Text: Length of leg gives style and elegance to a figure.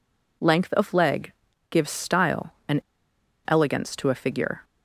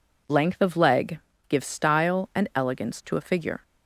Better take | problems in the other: second | pauses between "leg" and "gives"; at 1.3 s; 0.38 s long; slight in the second // pauses between "and" and "elegance"; noticeable; at 2.8 s; 0.64 s long

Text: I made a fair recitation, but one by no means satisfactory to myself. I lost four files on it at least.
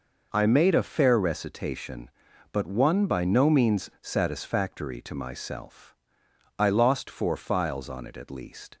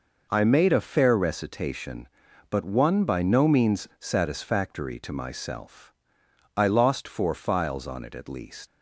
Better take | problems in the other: first | leaves "least" unfinished; at 8.6 s; 80 ms

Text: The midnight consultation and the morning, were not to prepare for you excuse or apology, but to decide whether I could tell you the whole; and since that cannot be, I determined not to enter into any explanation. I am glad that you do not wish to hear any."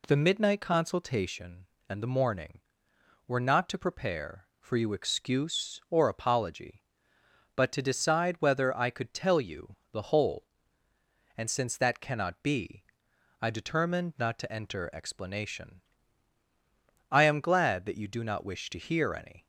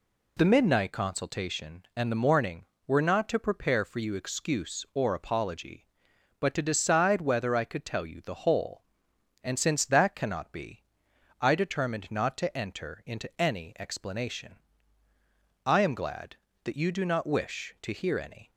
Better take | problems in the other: second | pauses between "you" and "the"; slight; at 9.7 s; 0.16 s long // skips "into any"; at 14.9 s

